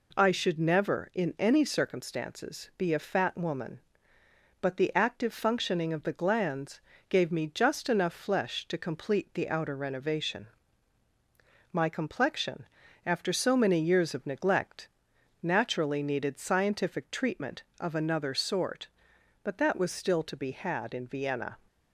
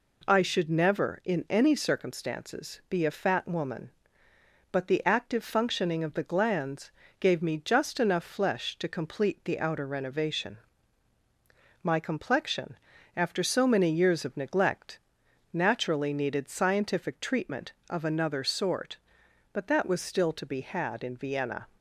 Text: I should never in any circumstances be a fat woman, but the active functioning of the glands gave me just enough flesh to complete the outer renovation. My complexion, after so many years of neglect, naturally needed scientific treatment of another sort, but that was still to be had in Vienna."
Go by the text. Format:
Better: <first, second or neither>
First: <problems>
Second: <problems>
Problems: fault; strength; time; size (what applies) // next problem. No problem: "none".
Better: neither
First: pauses between "glands" and "gave"; slight; at 6.8 s; 0.28 s long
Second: pauses between "glands" and "gave"; slight; at 6.9 s; 0.28 s long